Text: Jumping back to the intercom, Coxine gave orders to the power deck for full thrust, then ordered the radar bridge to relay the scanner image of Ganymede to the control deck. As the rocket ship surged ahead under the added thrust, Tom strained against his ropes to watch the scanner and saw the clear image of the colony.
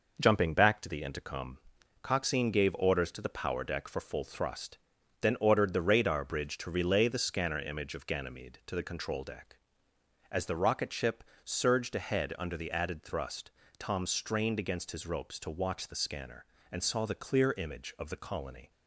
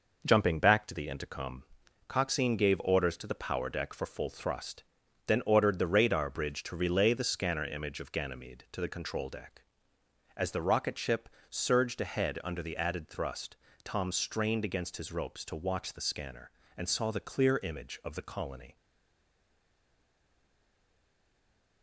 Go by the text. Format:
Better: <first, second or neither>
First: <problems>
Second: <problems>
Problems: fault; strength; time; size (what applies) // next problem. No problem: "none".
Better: first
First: pauses between "ship" and "surged"; slight; at 11.2 s; 0.22 s long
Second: pauses between "ship" and "surged"; slight; at 11.2 s; 0.22 s long // stays silent after the last word; strong; from 18.7 s on; 3.1 s long